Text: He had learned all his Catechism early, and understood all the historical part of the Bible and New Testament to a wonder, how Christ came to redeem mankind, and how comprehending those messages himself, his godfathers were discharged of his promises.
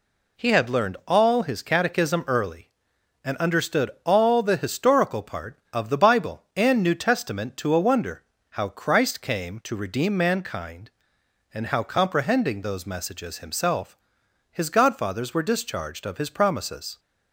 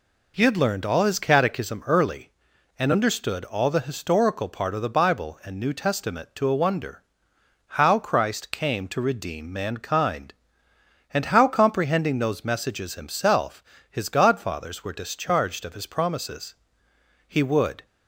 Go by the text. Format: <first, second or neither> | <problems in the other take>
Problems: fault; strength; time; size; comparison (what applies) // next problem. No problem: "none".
first | goes on to say "He would"; from 17.2 s on; 0.56 s long